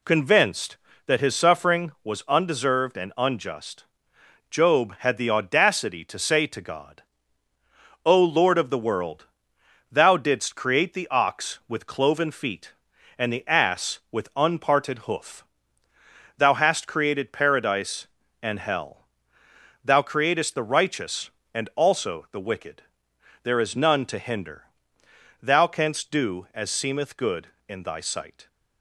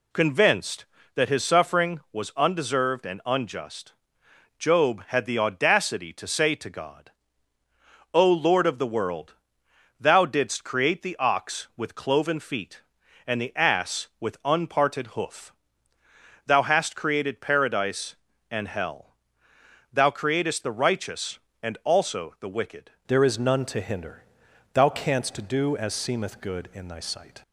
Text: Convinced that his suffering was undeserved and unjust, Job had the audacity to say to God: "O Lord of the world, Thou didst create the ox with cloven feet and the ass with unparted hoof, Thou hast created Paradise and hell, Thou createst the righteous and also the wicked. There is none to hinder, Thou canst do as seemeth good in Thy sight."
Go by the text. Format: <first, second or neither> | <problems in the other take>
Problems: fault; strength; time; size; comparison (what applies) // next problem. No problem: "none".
first | changes voice at "There"; from 23.0 s on; 4.4 s long